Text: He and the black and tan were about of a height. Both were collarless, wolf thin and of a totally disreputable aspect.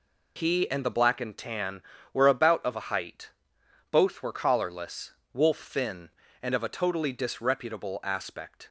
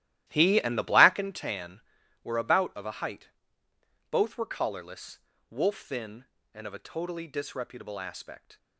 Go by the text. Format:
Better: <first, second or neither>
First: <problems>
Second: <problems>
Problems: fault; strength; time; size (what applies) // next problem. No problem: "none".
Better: first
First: none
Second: starts louder than the rest; strong; until 1.4 s; 14 dB